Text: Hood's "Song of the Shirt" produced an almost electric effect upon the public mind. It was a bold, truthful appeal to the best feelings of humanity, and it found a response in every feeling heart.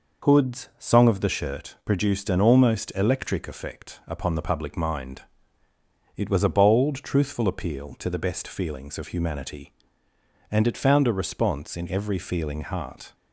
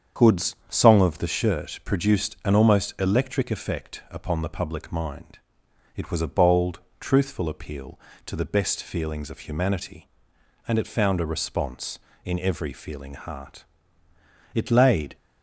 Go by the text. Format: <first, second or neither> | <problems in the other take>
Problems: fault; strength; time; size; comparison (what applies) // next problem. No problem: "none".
first | starts louder than the rest; strong; until 1.3 s; 7.5 dB // pauses between "Hood's" and "Song"; slight; at 0.5 s; 0.16 s long // goes on to say "It laid"; noticeable; from 14.5 s on; 0.62 s long